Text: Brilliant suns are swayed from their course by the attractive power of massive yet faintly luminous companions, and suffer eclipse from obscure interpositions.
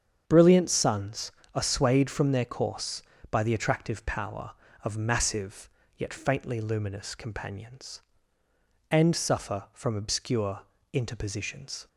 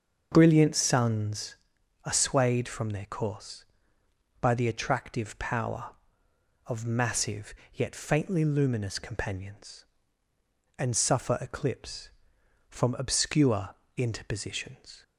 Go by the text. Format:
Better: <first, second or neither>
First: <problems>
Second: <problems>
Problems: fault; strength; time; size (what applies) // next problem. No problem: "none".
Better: second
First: starts louder than the rest; strong; until 1.2 s; 7.5 dB // pauses between "massive" and "yet"; slight; at 5.6 s; 0.28 s long // skips "eclipse"; at 9.6 s // pauses between "obscure" and "interpositions"; slight; at 10.6 s; 0.30 s long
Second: starts louder than the rest; until 1.3 s; 6.5 dB // pauses between "massive" and "yet"; slight; at 7.5 s; 0.22 s long // pauses between "obscure" and "interpositions"; slight; at 13.7 s; 0.20 s long